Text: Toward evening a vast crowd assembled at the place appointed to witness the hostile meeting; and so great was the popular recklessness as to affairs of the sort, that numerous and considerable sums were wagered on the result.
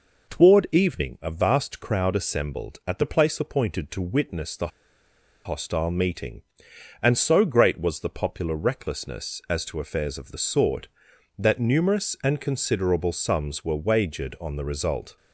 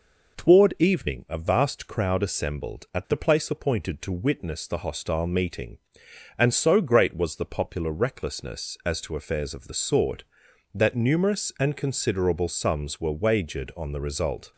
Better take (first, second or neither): second